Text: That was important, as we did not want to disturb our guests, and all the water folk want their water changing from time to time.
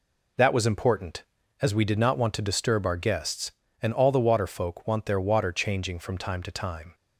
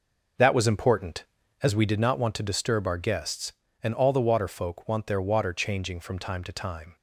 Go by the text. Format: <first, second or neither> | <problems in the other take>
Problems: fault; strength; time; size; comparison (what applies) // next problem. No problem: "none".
first | starts louder than the rest; noticeable; until 2.1 s; 6 dB